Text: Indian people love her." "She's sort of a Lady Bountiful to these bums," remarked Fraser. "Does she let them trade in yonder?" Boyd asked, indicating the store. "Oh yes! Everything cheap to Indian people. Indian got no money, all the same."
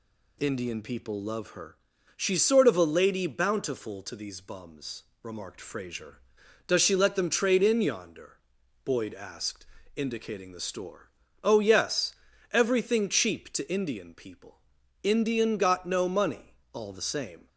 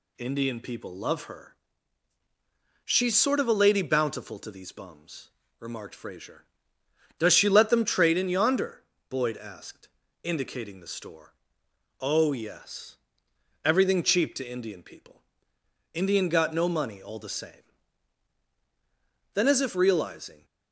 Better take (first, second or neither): first